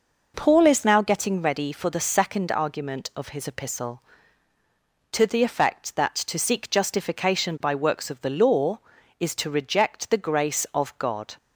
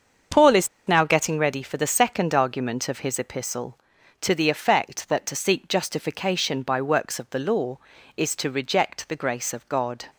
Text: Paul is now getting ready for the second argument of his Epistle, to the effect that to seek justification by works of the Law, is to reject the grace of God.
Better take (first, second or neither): first